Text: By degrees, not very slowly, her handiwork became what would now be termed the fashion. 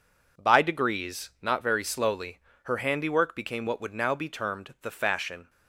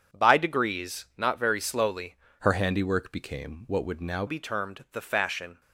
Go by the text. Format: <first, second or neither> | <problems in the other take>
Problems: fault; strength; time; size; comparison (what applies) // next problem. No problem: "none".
first | starts louder than the rest; strong; until 1.2 s; 8 dB // changes voice from "her" to "now"; from 2.3 to 4.2 s; 1.9 s long